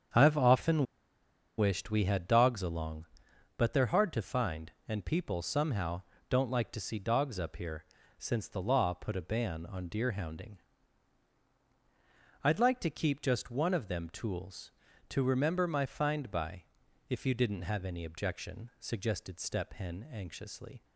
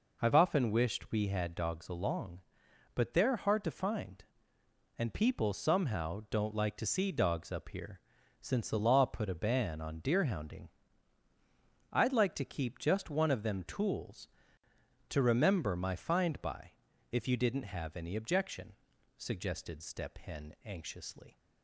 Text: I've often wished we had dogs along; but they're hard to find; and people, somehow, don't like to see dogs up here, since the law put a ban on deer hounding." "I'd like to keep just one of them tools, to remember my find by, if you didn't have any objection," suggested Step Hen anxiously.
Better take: second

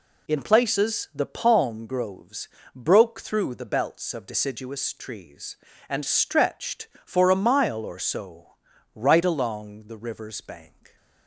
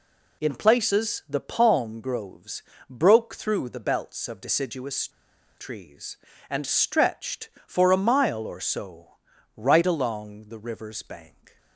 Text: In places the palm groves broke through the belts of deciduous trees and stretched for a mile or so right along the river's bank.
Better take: first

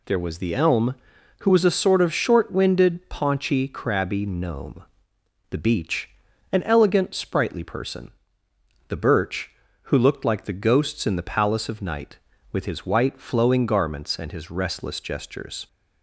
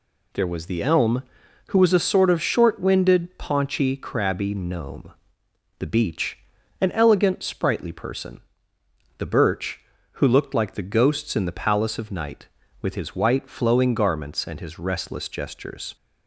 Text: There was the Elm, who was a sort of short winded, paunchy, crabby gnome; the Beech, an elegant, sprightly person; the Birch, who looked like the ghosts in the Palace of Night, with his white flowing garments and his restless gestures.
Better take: neither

